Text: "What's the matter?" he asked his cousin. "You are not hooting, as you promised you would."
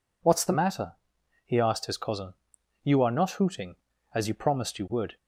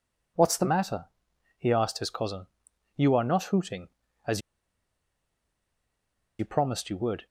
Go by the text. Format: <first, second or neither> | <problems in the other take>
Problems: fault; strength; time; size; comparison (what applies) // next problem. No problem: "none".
first | pauses between "as" and "you"; strong; at 4.3 s; 1.9 s long